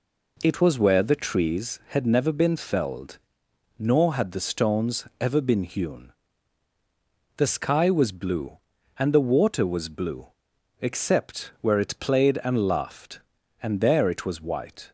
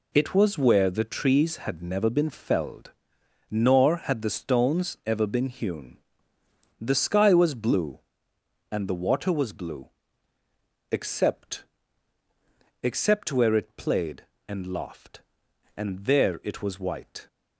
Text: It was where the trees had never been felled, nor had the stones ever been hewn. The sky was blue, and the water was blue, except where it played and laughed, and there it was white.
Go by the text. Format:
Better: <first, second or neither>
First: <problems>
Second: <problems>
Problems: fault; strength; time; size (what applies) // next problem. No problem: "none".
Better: first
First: none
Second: says "except" twice; at 12.8 s